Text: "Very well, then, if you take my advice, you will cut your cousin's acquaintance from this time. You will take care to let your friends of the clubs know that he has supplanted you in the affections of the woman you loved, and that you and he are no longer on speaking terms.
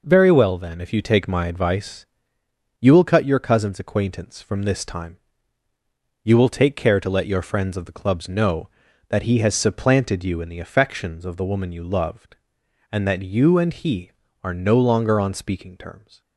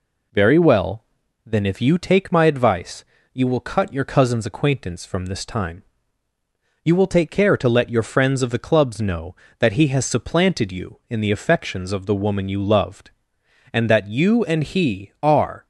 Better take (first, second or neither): first